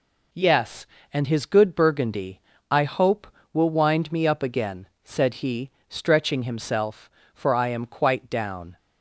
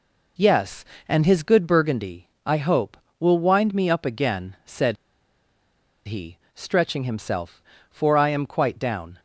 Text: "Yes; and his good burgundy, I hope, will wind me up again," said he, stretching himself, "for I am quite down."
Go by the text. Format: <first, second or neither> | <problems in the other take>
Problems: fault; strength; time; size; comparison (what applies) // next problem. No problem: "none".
first | pauses between "said" and "he"; at 4.9 s; 1.1 s long